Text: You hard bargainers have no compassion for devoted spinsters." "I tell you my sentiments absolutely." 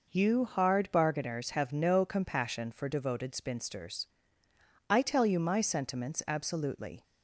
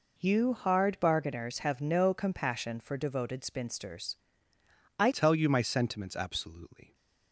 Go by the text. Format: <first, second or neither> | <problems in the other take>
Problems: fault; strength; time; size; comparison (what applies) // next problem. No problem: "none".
first | changes voice at "tell"; from 5.1 s on; 1.8 s long